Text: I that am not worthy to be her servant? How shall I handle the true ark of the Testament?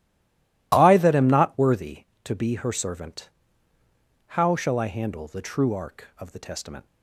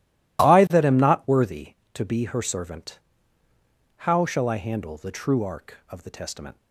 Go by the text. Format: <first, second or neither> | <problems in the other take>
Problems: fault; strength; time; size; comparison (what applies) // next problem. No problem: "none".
second | stays silent before the first word; slight; until 0.7 s; 0.7 s long